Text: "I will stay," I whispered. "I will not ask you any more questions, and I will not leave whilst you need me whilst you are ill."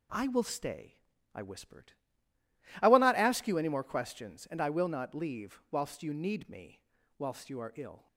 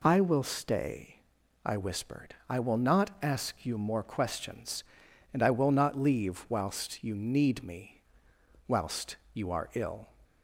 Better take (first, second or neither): first